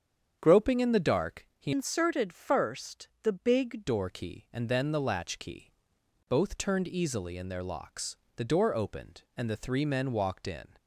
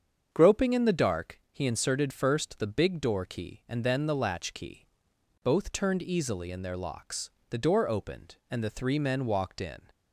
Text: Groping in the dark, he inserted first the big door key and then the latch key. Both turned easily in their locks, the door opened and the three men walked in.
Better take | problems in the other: second | starts louder than the rest; strong; until 1.4 s; 8 dB; strong in the second // changes voice from "inserted" to "big"; from 1.7 to 3.8 s; 2.1 s long

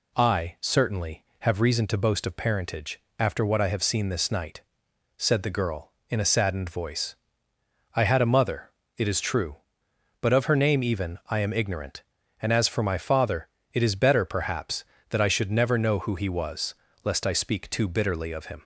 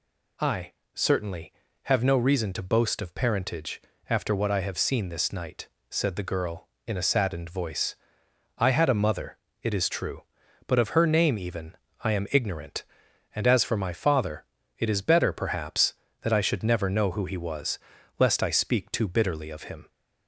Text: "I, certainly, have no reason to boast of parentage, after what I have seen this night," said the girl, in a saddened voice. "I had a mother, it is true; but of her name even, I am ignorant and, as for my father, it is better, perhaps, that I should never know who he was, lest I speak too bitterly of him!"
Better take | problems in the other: second | skips "no"; at 1.6 s

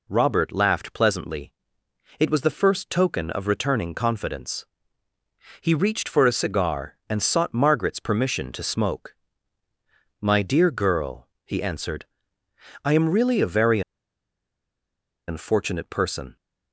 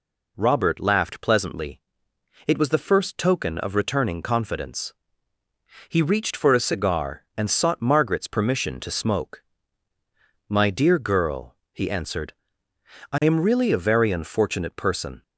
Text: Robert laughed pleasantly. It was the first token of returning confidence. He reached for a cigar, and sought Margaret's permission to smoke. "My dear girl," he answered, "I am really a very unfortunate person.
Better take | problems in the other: second | pauses between "very" and "unfortunate"; strong; at 13.8 s; 1.4 s long

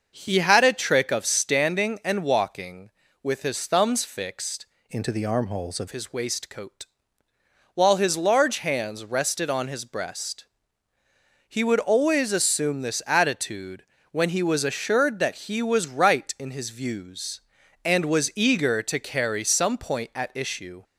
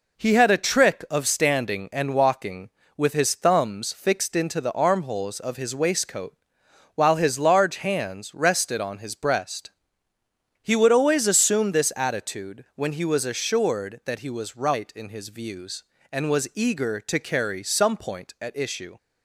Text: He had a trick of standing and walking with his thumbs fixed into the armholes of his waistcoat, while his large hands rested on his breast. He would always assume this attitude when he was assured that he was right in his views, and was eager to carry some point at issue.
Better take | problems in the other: second | starts louder than the rest; noticeable; until 1.1 s; 6 dB // changes voice from "into" to "of"; from 4.8 to 5.8 s; 1.0 s long // pauses between "attitude" and "when"; slight; at 13.8 s; 0.28 s long

